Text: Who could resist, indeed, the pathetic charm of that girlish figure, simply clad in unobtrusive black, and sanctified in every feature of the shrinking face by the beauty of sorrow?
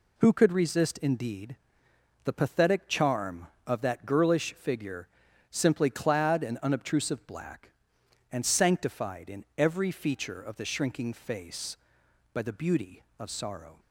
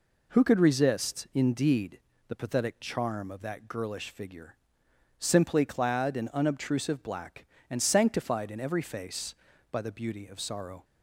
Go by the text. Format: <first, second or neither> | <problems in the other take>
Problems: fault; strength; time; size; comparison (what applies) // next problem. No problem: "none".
first | skips "feature of the shrinking"; at 8.8 s